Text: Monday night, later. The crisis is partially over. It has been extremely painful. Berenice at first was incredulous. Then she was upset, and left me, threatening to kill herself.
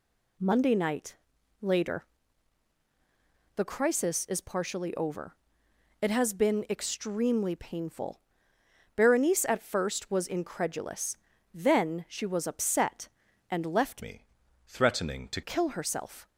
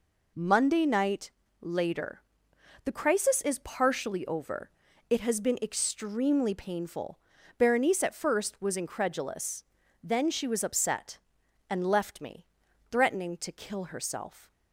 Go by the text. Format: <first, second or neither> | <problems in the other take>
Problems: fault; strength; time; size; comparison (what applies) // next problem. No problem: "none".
second | changes voice from "me" to "to"; from 14.0 to 15.4 s; 1.4 s long